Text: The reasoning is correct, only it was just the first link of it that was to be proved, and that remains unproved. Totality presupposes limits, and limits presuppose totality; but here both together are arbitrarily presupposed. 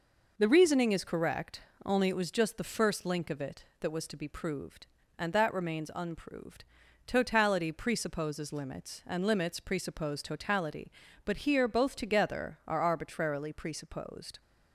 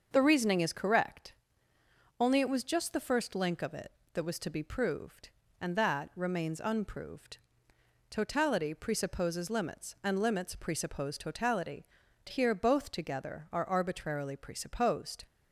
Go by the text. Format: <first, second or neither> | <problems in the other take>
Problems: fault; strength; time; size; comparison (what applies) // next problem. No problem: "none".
first | starts louder than the rest; until 1.1 s; 6.5 dB // skips "but"; at 12.0 s